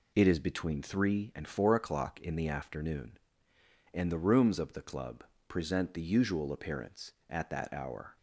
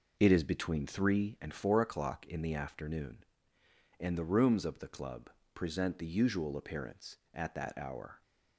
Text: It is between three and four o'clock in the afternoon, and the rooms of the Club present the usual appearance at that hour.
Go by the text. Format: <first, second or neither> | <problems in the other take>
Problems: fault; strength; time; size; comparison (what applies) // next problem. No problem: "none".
first | starts louder than the rest; noticeable; until 1.8 s; 5.5 dB // pauses between "Club" and "present"; slight; at 5.2 s; 0.24 s long; slight in the first